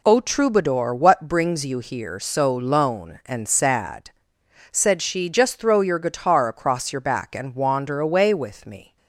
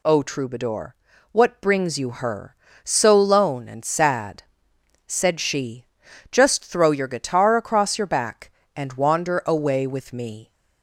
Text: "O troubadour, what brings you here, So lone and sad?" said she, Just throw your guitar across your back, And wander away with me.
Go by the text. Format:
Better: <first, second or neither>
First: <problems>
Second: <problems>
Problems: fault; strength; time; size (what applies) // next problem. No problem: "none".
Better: first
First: none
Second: says "her" for "here"; at 2.1 s